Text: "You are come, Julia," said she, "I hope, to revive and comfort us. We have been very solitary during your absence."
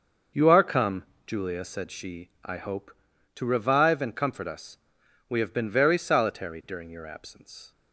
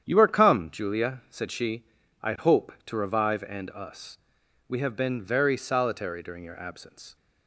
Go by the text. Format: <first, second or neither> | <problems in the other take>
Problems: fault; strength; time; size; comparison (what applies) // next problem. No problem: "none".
first | starts louder than the rest; strong; until 1.0 s; 9 dB; also in the first // skips "comfort"; at 3.7 s